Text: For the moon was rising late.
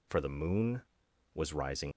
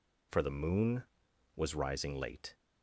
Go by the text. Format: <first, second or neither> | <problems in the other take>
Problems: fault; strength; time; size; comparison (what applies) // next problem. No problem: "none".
second | stops before "late"; at 1.9 s